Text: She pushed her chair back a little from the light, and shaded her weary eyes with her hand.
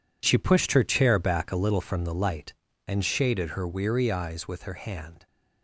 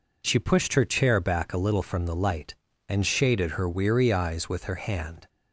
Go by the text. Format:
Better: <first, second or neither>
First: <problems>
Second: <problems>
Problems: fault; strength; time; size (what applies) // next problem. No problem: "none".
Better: second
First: gets quieter; strong; throughout; 11.5 dB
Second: none